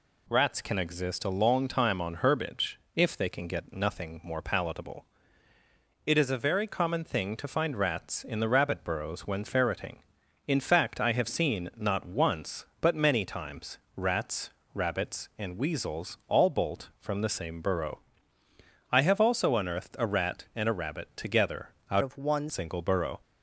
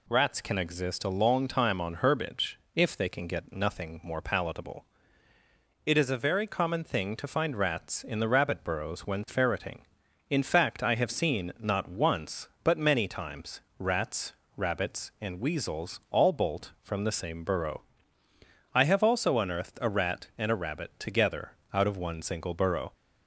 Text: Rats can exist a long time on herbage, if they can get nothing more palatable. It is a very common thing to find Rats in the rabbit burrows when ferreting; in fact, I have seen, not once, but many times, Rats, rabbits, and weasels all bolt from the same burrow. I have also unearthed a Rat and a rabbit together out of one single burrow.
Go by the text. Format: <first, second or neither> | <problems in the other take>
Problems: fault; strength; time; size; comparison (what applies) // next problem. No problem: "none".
second | pauses between "together" and "out"; slight; at 21.6 s; 0.20 s long; slight in the second // changes voice from "of" to "one"; from 22.0 to 22.4 s; 0.4 s long